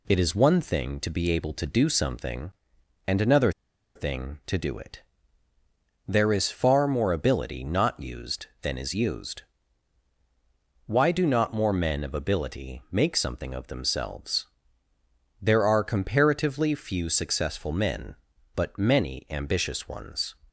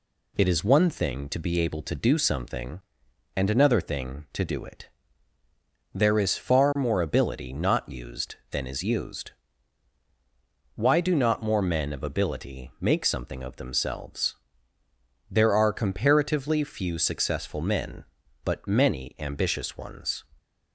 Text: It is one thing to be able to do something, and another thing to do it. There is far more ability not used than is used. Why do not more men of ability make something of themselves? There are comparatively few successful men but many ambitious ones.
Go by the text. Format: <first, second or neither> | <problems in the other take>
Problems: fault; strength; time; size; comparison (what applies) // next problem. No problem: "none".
second | pauses between "another" and "thing"; at 3.4 s; 0.45 s long